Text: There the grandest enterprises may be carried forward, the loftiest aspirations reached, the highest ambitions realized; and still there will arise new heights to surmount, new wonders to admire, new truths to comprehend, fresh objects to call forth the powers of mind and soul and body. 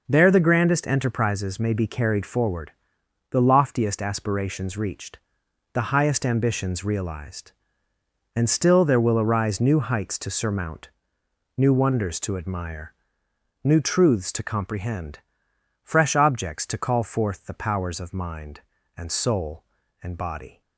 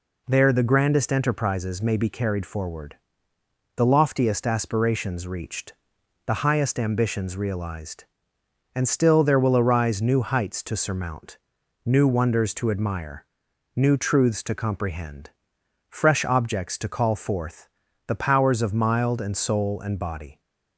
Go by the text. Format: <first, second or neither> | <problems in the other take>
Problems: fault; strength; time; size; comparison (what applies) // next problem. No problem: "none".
first | pauses between "forth" and "the"; at 17.6 s; 0.38 s long // says "mild" for "mind"; at 18.7 s